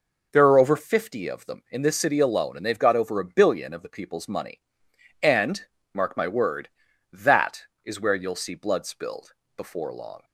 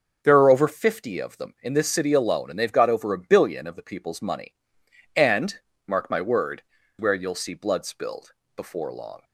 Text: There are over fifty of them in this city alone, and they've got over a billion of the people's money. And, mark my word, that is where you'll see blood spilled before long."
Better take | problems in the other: first | starts louder than the rest; until 1.2 s; 6.5 dB // skips "that is"; at 6.8 s // pauses between "spilled" and "before"; slight; at 8.3 s; 0.22 s long; slight in the first

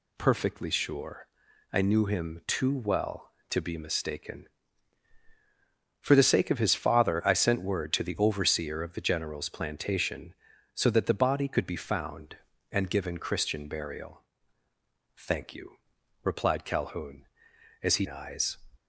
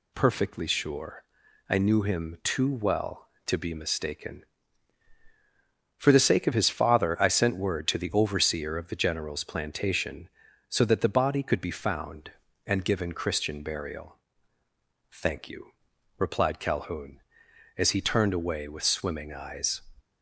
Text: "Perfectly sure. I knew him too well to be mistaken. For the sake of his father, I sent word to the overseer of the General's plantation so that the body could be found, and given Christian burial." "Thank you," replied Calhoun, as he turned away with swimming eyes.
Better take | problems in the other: second | skips "turned away with swimming"; at 18.0 s

